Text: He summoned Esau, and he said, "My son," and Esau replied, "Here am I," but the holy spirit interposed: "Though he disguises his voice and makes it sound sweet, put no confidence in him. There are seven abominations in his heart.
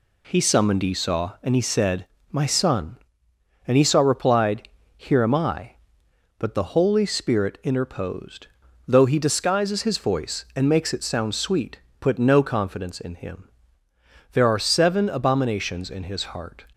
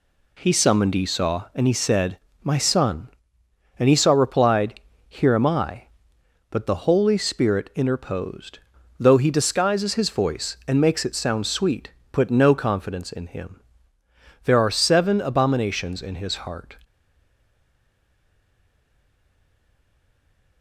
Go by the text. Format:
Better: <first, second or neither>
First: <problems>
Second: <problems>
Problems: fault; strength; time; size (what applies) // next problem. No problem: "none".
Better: first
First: none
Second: stays silent after the last word; strong; from 16.8 s on; 3.8 s long